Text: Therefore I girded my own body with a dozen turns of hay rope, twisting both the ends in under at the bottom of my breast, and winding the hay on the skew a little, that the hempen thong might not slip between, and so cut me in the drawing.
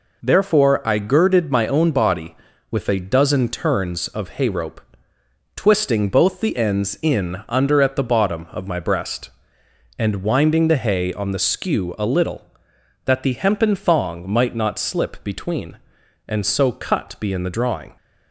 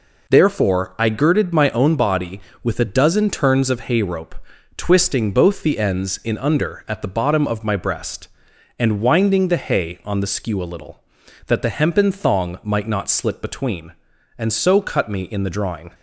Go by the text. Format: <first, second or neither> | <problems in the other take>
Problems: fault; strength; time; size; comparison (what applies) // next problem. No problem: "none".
second | says "be" for "me"; at 17.2 s